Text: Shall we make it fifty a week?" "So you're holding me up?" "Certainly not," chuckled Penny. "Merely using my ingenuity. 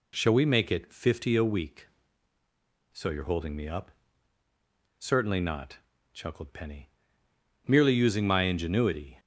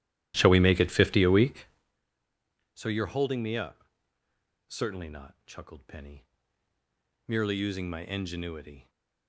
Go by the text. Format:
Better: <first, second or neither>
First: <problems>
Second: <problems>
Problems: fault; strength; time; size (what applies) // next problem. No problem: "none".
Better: first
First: none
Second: starts louder than the rest; strong; until 1.9 s; 13.5 dB